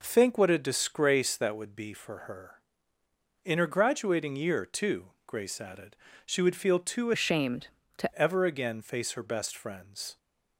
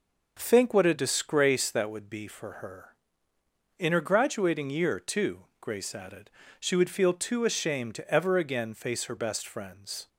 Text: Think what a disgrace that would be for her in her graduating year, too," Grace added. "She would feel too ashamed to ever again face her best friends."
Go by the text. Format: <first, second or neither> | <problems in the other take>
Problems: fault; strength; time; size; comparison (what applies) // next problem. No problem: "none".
second | changes voice from "ashamed" to "to"; from 7.1 to 8.1 s; 1.0 s long